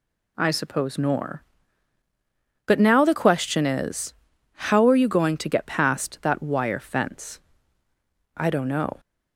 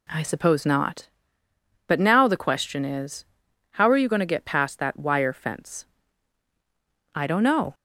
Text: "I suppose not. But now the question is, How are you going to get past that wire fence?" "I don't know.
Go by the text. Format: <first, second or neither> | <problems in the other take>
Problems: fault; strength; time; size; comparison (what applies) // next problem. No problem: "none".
second | says "nor" for "not"; at 0.9 s